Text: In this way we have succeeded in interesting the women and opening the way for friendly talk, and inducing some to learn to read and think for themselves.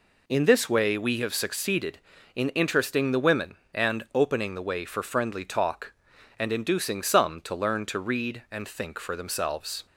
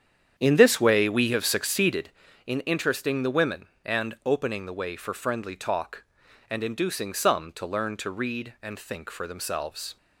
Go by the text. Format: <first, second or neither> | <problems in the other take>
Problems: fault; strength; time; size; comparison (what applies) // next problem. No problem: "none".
first | starts louder than the rest; strong; until 2.3 s; 8.5 dB